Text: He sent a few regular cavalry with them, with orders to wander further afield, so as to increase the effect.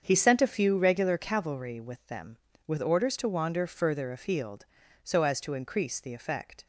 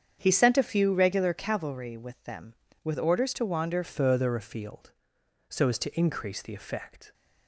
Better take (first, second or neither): first